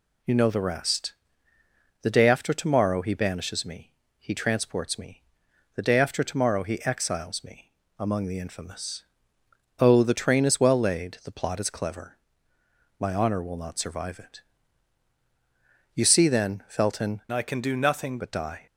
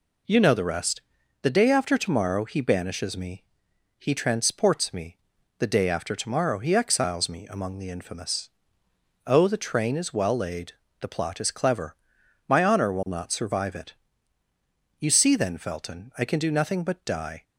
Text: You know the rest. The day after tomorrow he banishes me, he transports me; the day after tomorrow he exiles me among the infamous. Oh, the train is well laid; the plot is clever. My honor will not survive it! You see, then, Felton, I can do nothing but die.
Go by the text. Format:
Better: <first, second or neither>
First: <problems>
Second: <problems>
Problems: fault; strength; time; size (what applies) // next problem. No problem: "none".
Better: second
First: pauses between "me" and "among"; slight; at 7.7 s; 0.28 s long // changes voice from "I" to "nothing"; from 17.3 to 18.1 s; 0.8 s long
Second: none